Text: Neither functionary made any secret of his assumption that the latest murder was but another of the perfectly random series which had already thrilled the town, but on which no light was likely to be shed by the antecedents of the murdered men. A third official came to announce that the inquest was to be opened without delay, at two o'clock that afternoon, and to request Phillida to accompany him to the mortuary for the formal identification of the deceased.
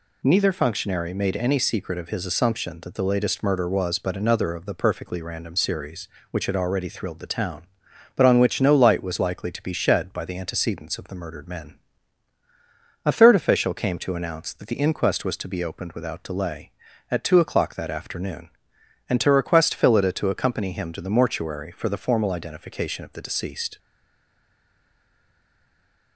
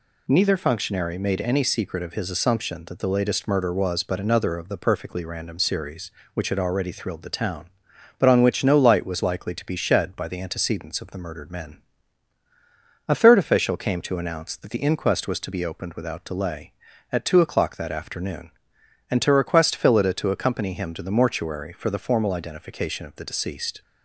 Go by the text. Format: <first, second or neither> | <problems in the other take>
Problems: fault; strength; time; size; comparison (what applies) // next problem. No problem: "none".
second | stays silent after the last word; from 23.7 s on; 2.4 s long